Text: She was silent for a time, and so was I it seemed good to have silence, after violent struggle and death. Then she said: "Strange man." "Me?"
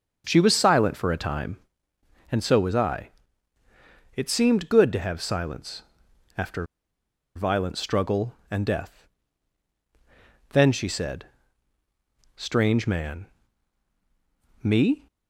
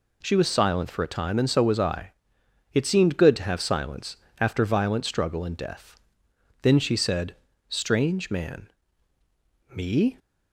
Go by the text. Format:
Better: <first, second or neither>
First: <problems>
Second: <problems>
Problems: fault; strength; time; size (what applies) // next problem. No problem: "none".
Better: second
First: starts louder than the rest; until 1.2 s; 6.5 dB // pauses between "I" and "it"; at 3.0 s; 1.0 s long // pauses between "after" and "violent"; noticeable; at 6.6 s; 0.70 s long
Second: pauses between "I" and "it"; noticeable; at 2.1 s; 0.60 s long